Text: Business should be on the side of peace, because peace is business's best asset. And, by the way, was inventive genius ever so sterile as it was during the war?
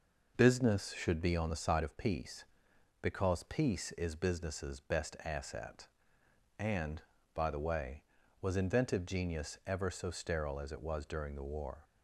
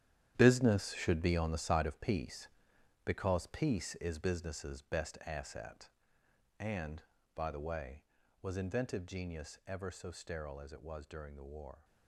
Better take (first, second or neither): first